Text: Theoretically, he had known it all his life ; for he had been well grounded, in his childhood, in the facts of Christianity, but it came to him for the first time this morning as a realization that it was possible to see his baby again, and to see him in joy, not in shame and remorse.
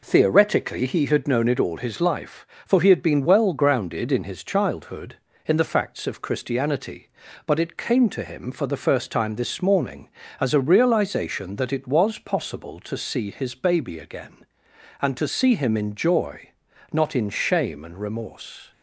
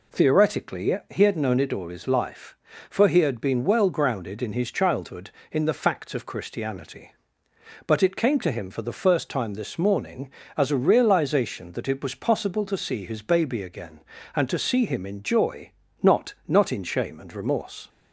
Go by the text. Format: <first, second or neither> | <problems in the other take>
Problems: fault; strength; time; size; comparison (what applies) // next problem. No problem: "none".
first | says "not" twice; at 16.4 s